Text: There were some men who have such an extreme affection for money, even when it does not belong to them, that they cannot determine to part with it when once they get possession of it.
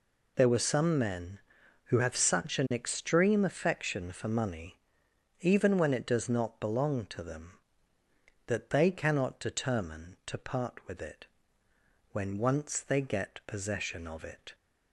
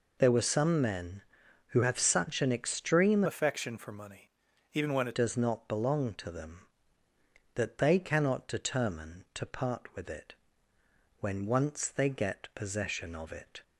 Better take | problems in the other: first | changes voice from "affection" to "it"; from 3.2 to 5.1 s; 1.9 s long // pauses between "it" and "when"; noticeable; at 10.3 s; 0.84 s long; noticeable in the first

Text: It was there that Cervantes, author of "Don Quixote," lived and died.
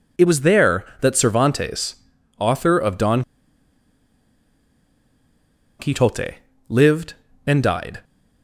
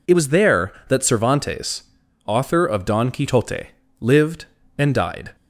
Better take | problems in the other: second | pauses between "Don" and "Quixote"; strong; at 3.2 s; 2.5 s long

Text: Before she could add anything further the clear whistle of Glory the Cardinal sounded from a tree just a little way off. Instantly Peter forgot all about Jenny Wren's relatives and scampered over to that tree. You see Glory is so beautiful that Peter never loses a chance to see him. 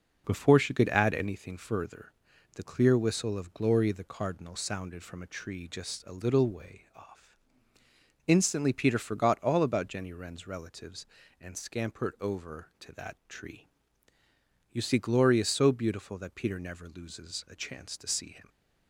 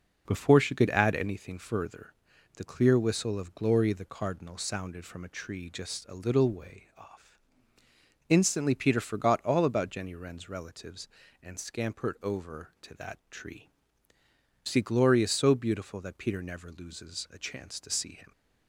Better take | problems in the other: first | pauses between "further" and "the"; at 2.1 s; 0.44 s long; also in the first // skips "You"; at 14.1 s

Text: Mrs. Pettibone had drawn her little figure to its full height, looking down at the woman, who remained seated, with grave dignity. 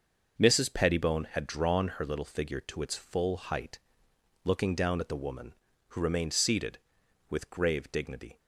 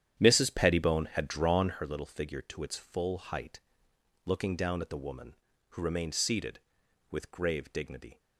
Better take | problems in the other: first | starts louder than the rest; strong; until 1.8 s; 9.5 dB

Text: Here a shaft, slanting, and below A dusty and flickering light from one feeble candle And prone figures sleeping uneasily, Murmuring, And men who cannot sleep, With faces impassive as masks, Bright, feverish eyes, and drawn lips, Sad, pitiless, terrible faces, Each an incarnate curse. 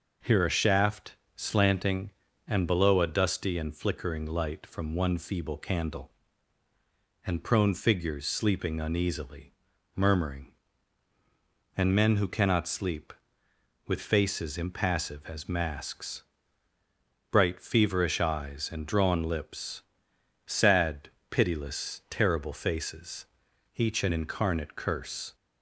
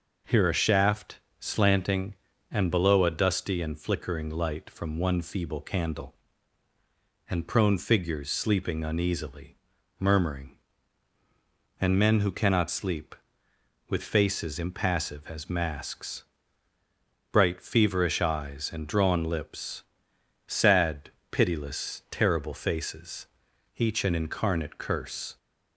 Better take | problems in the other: neither | none

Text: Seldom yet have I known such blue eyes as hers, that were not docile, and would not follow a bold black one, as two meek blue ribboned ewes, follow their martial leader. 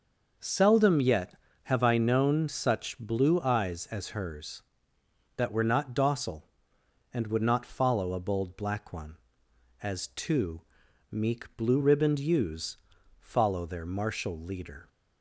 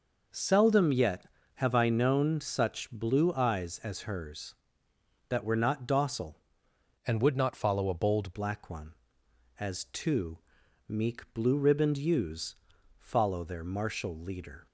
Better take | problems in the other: first | changes voice from "and" to "bold"; from 7.0 to 8.3 s; 1.3 s long // pauses between "two" and "meek"; noticeable; at 10.3 s; 0.48 s long; noticeable in the first

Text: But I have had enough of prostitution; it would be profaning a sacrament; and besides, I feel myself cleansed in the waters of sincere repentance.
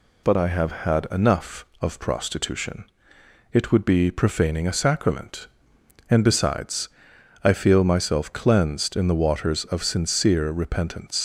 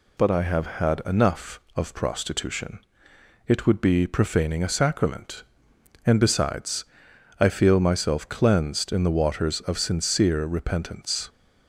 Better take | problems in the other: second | leaves "repentance" unfinished; at 11.1 s; 95 ms

